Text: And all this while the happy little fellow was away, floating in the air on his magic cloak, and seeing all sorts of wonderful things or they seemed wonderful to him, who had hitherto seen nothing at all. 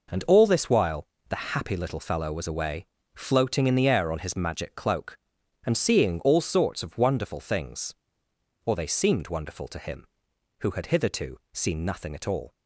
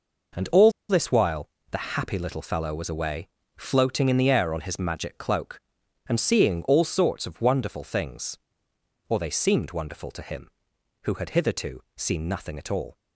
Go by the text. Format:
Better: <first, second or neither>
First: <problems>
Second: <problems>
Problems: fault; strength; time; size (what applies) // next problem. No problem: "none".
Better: first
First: pauses between "while" and "the"; slight; at 1.0 s; 0.24 s long // pauses between "hitherto" and "seen"; slight; at 11.3 s; 0.16 s long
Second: pauses between "all" and "this"; slight; at 0.7 s; 0.17 s long // pauses between "while" and "the"; slight; at 1.4 s; 0.24 s long // pauses between "hitherto" and "seen"; slight; at 11.8 s; 0.16 s long